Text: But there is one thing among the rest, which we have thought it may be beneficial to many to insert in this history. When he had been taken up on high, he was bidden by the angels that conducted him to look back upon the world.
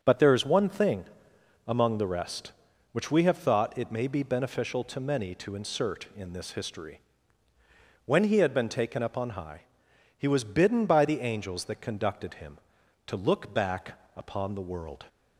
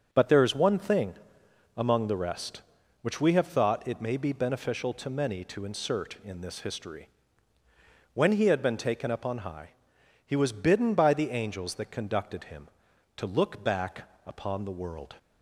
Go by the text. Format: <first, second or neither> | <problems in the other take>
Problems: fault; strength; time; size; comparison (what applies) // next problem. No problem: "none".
neither | starts louder than the rest; the same in both // pauses between "thing" and "among"; noticeable; the same in both // pauses between "back" and "upon"; slight; the same in both